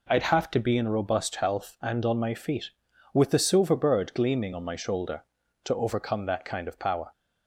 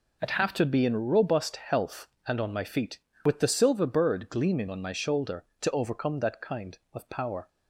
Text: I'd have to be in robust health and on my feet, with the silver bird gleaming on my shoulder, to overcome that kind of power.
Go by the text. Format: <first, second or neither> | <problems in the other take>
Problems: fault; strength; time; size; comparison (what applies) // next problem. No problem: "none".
neither | none